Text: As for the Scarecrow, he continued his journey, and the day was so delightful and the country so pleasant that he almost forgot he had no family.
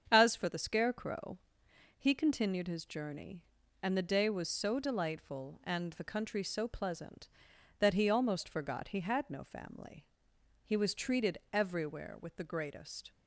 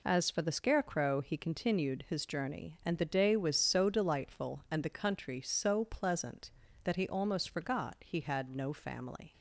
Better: second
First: starts louder than the rest; strong; until 1.1 s; 7.5 dB // goes on to say "He was treated everywhere with the greatest"; strong; from 10.6 s on; 2.4 s long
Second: none

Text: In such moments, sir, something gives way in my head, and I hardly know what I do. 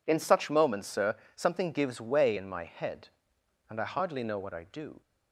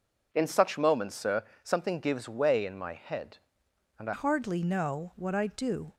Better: first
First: none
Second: changes voice at "hardly"; from 4.1 s on; 1.8 s long

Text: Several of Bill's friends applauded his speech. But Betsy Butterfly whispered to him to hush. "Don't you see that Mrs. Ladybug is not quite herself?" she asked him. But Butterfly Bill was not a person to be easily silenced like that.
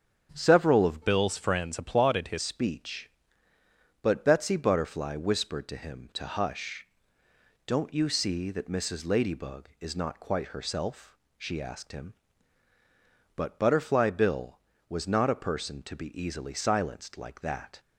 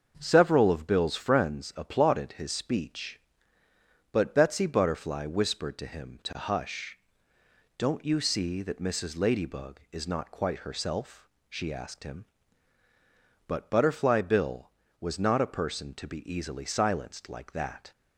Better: second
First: starts louder than the rest; strong; until 1.3 s; 8 dB // changes voice from "Bill's" to "his"; from 1.0 to 2.3 s; 1.3 s long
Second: starts louder than the rest; until 1.1 s; 6.5 dB

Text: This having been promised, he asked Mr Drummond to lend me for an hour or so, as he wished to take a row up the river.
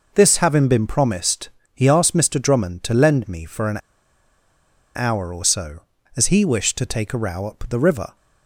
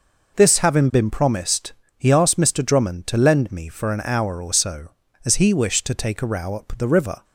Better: second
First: pauses between "an" and "hour"; at 3.7 s; 1.1 s long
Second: none

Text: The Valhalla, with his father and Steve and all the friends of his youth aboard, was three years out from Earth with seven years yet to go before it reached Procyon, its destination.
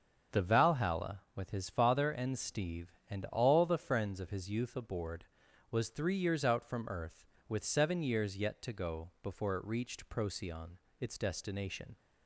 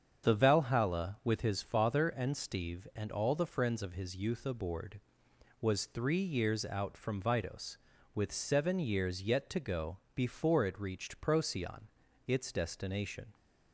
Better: first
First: starts louder than the rest; until 1.4 s; 7 dB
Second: starts louder than the rest; strong; until 1.2 s; 7.5 dB // says "Vidos" for "Earth"; at 7.2 s // pauses between "go" and "before"; slight; at 9.9 s; 0.16 s long

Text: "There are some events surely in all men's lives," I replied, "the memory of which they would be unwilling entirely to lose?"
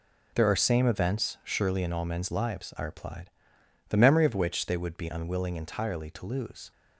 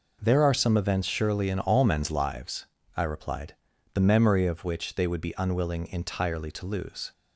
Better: second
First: says "same" for "some"; at 0.5 s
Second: none

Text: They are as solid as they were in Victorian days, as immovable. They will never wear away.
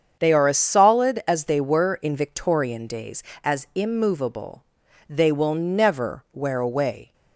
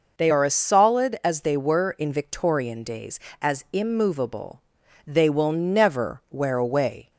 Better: second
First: gets quieter; strong; throughout; 9.5 dB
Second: none

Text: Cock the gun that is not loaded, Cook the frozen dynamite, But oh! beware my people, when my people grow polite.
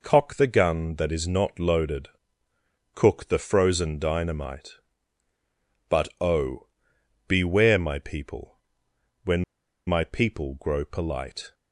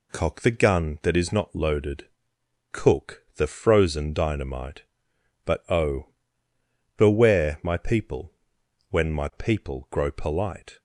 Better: second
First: pauses between "when" and "my"; at 9.4 s; 0.44 s long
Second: none

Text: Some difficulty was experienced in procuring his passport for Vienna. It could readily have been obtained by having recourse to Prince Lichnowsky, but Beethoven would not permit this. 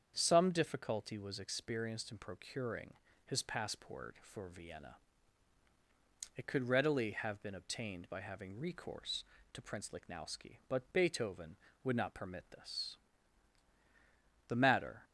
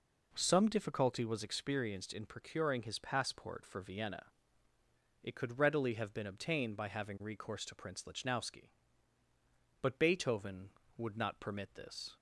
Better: second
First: starts louder than the rest; strong; until 1.1 s; 7.5 dB // pauses between "procuring" and "his"; slight; at 2.9 s; 0.34 s long // goes on to say "The matter"; from 14.4 s on; 0.58 s long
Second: none

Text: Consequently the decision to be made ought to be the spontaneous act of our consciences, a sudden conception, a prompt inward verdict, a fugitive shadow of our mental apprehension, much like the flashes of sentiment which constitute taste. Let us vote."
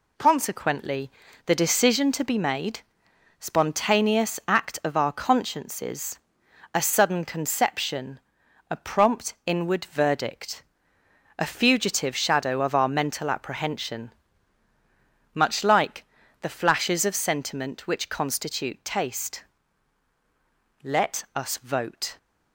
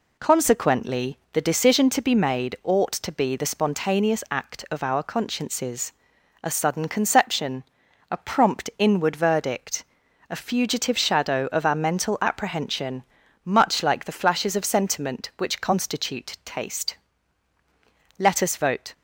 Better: second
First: pauses between "Consequently" and "the"; slight; at 1.0 s; 0.36 s long // skips "ought to be the"; at 3.0 s // pauses between "like" and "the"; slight; at 16.0 s; 0.36 s long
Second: pauses between "Consequently" and "the"; slight; at 1.1 s; 0.16 s long

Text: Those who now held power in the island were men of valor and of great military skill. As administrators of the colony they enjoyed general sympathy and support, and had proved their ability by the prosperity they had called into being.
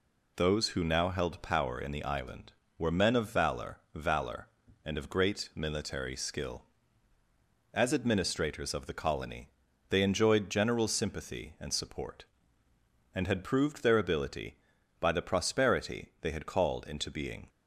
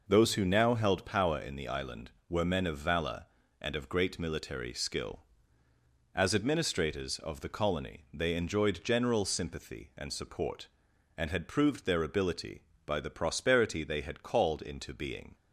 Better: second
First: says "valor" twice; at 3.9 s // pauses between "colony" and "they"; at 9.4 s; 0.42 s long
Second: none

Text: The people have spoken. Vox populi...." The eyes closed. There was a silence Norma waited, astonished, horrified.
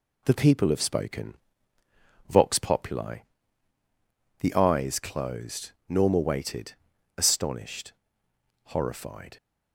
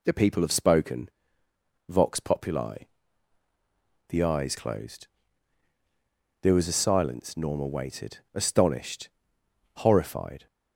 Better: second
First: skips "There was a silence"; at 5.7 s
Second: none

